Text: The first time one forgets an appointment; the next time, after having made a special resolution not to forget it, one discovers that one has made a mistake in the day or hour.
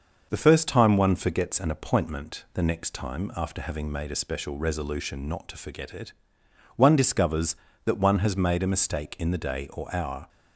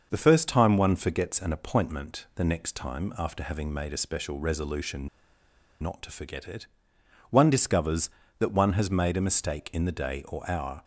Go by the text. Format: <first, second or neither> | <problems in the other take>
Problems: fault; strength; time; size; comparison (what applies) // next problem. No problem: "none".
first | starts louder than the rest; until 1.1 s; 6 dB; also in the first // pauses between "resolution" and "not"; noticeable; at 5.0 s; 0.73 s long